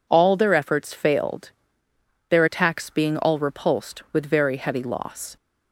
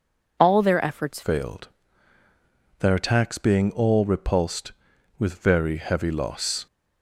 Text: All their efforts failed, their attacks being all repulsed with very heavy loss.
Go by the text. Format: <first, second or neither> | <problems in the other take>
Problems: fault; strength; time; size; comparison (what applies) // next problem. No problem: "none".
first | changes voice at "failed"; from 1.2 s on; 5.4 s long